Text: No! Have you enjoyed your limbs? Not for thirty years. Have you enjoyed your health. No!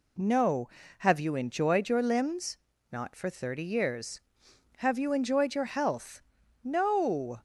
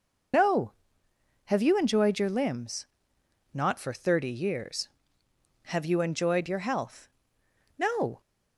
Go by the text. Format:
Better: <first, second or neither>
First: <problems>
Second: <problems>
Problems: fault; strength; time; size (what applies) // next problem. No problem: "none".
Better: first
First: none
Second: loses the start of "No"; at 0.3 s; 20 ms